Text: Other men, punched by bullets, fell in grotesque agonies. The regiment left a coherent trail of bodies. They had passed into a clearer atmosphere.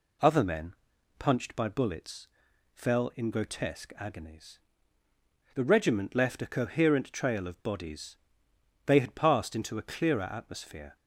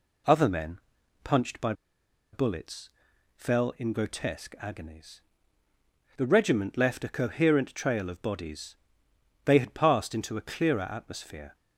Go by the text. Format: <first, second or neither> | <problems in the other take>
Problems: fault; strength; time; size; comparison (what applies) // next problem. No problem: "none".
first | pauses between "by" and "bullets"; noticeable; at 1.7 s; 0.59 s long